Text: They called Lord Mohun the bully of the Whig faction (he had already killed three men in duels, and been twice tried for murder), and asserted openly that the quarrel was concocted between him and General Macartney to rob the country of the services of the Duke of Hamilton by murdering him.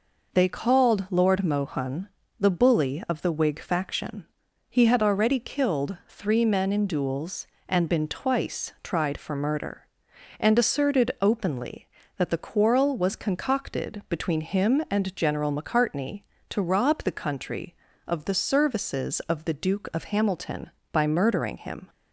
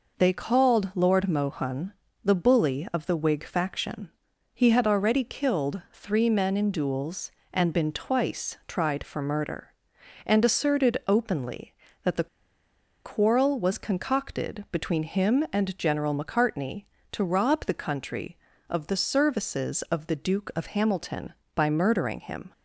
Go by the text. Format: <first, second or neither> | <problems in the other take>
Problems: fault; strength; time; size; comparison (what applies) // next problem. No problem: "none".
first | pauses between "Mohun" and "the"; slight; at 1.9 s; 0.30 s long; slight in the first // pauses between "the" and "quarrel"; noticeable; at 12.2 s; 0.76 s long